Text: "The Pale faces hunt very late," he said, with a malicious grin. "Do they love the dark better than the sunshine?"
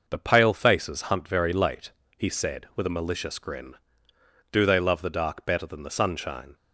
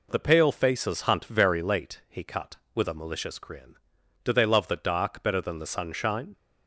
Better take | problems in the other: first | says "cut" for "said"; at 2.2 s

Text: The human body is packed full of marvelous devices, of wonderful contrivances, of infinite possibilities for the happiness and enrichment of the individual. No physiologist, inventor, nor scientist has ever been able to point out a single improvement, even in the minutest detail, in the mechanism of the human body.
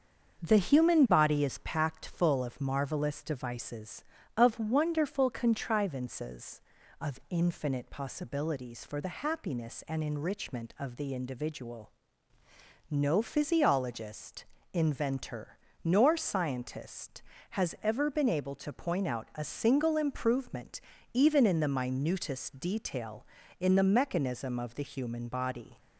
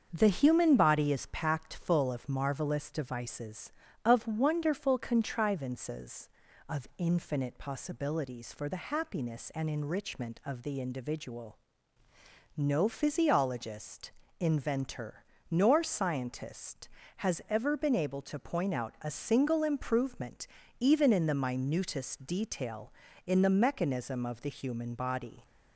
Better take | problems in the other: neither | starts louder than the rest; the same in both

